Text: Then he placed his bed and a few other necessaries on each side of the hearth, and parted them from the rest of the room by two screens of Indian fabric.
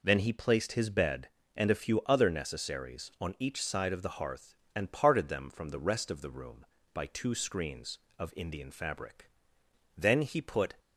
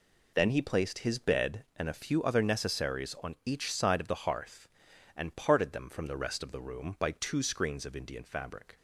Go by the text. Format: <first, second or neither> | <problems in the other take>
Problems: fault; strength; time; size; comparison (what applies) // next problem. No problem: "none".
second | goes on to say "Then he put"; noticeable; from 9.9 s on; 0.78 s long